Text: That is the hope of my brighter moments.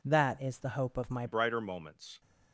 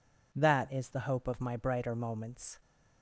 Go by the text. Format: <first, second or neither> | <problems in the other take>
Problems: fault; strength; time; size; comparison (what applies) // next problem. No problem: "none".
second | changes voice at "brighter"; from 1.2 s on; 1.0 s long